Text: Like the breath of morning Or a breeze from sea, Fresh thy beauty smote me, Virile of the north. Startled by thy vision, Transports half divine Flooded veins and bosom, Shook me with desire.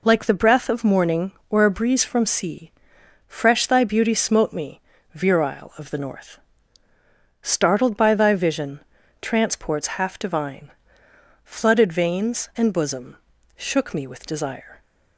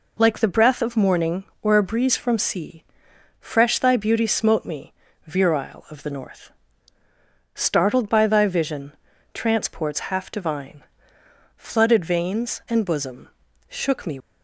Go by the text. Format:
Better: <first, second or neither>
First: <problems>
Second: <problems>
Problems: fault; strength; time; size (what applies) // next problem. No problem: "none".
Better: first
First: pauses between "divine" and "Flooded"; noticeable; at 10.6 s; 0.74 s long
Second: pauses between "divine" and "Flooded"; noticeable; at 10.8 s; 0.74 s long // stops before "with desire"; at 14.1 s